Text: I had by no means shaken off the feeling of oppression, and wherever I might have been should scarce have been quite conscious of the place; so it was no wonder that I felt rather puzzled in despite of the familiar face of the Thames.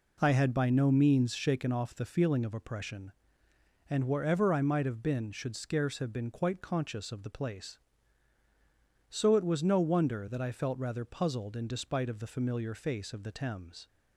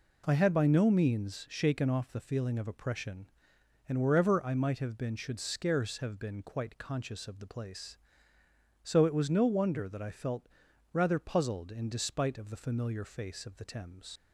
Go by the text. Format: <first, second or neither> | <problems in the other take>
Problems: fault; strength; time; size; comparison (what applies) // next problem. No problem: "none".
first | pauses between "felt" and "rather"; noticeable; at 10.4 s; 0.46 s long // leaves "Thames" unfinished; at 14.1 s; 75 ms